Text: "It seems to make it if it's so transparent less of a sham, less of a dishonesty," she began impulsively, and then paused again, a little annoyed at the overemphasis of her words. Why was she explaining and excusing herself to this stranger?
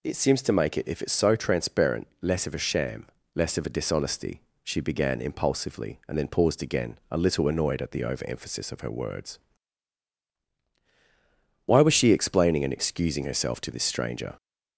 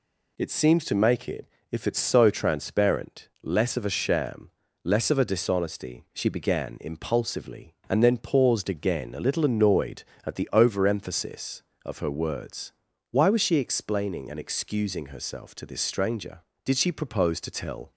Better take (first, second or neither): first